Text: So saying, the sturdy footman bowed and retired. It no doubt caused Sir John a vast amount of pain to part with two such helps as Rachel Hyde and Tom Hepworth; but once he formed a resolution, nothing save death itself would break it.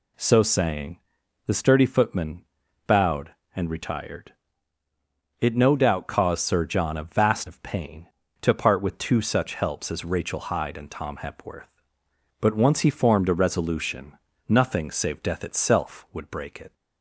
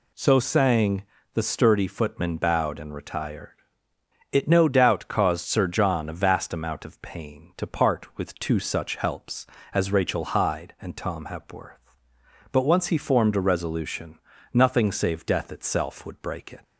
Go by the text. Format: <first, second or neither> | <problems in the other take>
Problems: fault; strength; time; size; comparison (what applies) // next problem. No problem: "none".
second | pauses between "footman" and "bowed"; at 2.4 s; 0.44 s long // skips "amount"; at 7.4 s